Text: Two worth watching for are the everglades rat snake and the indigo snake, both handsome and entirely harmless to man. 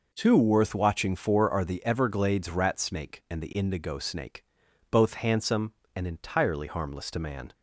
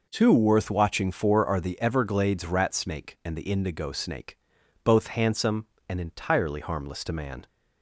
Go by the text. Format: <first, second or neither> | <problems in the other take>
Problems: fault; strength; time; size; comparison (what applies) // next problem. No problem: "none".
neither | none